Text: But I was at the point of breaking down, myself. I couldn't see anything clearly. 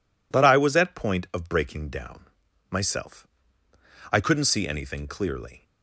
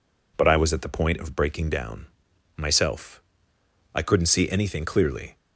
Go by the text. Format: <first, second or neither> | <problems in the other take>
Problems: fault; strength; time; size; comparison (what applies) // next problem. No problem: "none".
second | skips "the"; at 0.9 s